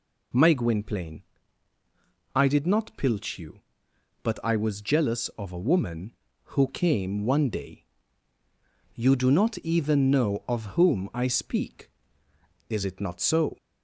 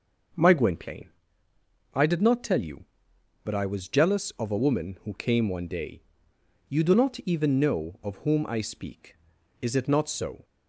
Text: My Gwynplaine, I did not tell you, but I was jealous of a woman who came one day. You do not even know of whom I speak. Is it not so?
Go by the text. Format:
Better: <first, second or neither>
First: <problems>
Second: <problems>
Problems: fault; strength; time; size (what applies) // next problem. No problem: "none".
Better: second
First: says "pilch" for "tell"; at 2.9 s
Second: none